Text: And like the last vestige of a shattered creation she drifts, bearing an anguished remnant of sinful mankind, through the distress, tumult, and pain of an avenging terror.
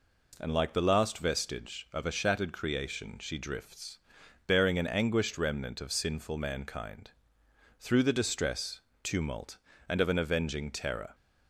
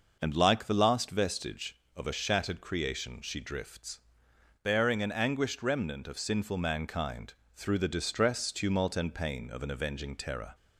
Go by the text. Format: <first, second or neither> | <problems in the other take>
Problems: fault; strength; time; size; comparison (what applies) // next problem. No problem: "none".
second | skips "pain"; at 10.0 s